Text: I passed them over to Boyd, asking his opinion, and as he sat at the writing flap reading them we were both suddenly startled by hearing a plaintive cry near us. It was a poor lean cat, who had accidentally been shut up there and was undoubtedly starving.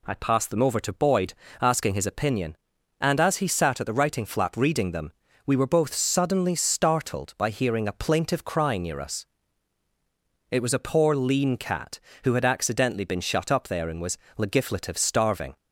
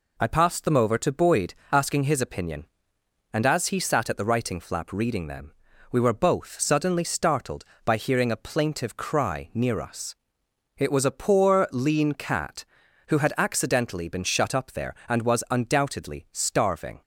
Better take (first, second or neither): second